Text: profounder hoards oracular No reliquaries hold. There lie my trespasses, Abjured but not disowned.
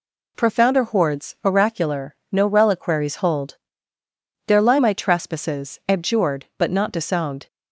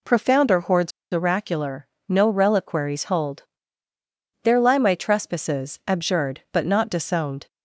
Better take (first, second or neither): first